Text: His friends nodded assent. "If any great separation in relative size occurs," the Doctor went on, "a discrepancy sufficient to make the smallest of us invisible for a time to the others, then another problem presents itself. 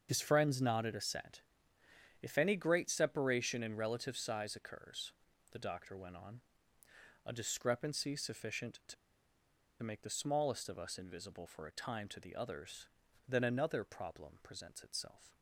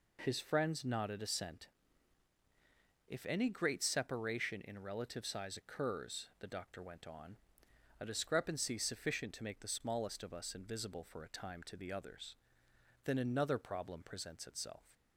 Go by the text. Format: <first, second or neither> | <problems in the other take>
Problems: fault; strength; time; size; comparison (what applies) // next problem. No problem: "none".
second | starts louder than the rest; until 1.1 s; 7 dB // pauses between "to" and "make"; noticeable; at 8.9 s; 0.88 s long